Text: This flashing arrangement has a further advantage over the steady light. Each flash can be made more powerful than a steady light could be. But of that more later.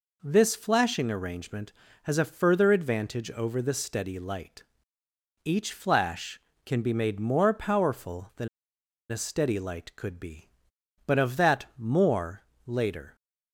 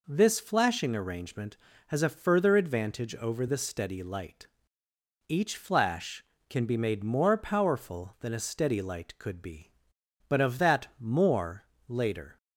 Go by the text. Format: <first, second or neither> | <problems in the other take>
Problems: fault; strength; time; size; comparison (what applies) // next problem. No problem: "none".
second | pauses between "than" and "a"; noticeable; at 8.4 s; 0.63 s long // pauses between "more" and "later"; slight; at 12.4 s; 0.24 s long; slight in the second